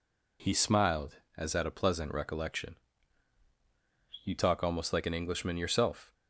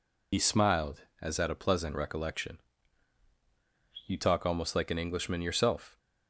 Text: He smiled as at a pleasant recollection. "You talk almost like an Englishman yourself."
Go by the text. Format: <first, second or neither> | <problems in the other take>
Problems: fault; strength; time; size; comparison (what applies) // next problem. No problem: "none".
first | loses the start of "He"; at 0.3 s; 70 ms